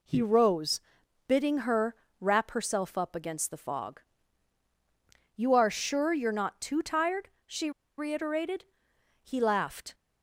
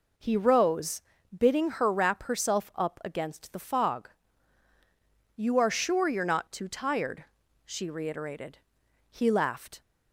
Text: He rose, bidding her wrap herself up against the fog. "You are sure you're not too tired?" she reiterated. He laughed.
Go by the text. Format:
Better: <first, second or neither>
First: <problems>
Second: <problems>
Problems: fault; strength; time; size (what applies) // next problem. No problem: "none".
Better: second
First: pauses between "her" and "wrap"; slight; at 1.9 s; 0.24 s long // pauses between "she" and "reiterated"; slight; at 7.7 s; 0.27 s long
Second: none